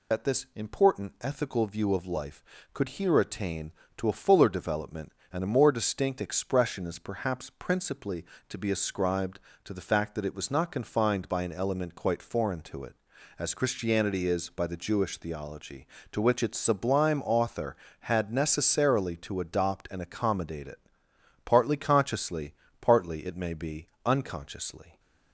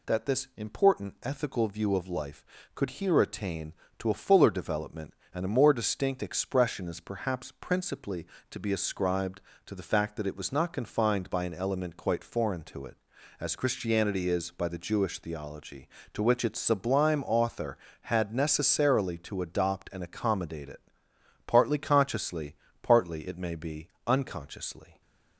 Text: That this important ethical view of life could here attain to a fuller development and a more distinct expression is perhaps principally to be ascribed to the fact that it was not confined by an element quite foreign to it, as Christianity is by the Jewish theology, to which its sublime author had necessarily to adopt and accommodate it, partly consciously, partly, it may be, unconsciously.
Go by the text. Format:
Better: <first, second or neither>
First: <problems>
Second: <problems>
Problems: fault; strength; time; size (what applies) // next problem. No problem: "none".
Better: second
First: loses the start of "That"; at 0.1 s; 55 ms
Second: none